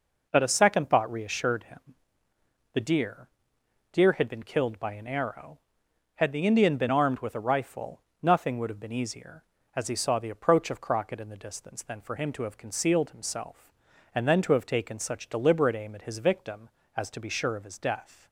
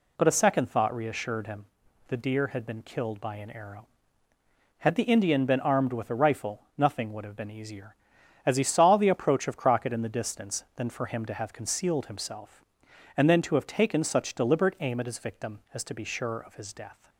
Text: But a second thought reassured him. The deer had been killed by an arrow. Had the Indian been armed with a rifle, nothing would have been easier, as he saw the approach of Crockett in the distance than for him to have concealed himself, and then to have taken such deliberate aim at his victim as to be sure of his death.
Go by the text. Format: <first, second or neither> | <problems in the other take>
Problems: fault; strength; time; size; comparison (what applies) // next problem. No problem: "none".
second | says "deer" twice; at 3.9 s